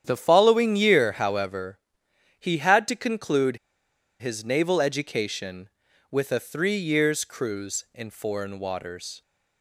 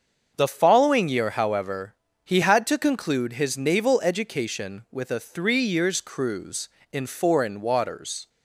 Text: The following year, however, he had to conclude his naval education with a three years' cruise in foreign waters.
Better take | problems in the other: second | starts louder than the rest; strong; until 1.0 s; 9.5 dB; also in the second // pauses between "conclude" and "his"; noticeable; at 3.5 s; 0.64 s long

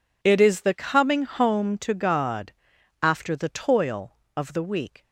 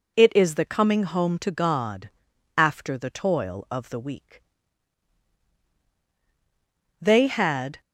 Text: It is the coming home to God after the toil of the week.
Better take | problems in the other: first | pauses between "God" and "after"; noticeable; at 2.1 s; 0.46 s long; noticeable in the first // goes on to say "They had"; noticeable; from 7.0 s on; 0.80 s long

